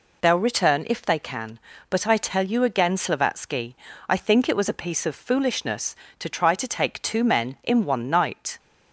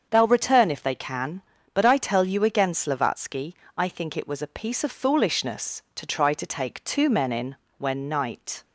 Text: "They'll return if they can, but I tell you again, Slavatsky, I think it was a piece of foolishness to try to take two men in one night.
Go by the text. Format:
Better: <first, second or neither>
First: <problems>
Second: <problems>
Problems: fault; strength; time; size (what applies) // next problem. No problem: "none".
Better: first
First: none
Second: starts louder than the rest; until 1.1 s; 7 dB // says "when" for "one"; at 7.7 s